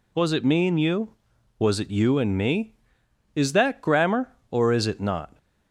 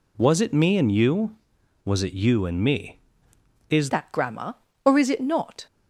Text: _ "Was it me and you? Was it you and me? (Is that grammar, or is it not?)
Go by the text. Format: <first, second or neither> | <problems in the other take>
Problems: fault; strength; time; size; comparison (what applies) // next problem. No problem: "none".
first | changes voice at "that"; from 3.8 s on; 1.8 s long